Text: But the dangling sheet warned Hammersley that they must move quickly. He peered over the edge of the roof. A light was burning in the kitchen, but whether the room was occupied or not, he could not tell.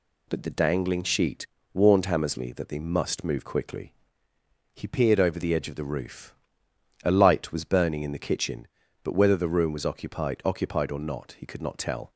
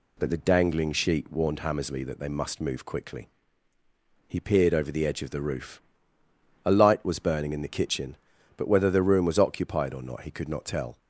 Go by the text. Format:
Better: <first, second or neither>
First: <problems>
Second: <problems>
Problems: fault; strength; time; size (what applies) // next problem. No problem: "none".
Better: second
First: pauses between "sheet" and "warned"; slight; at 1.4 s; 0.26 s long // says "occupied" twice; at 10.4 s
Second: none